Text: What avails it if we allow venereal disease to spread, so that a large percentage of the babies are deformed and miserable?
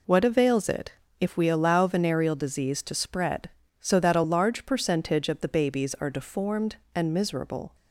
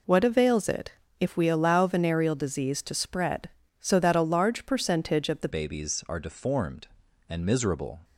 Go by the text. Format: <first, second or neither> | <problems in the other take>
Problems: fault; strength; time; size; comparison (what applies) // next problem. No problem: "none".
first | pauses between "it" and "if"; slight; at 0.9 s; 0.28 s long; slight in the first // changes voice at "babies"; from 5.4 s on; 2.5 s long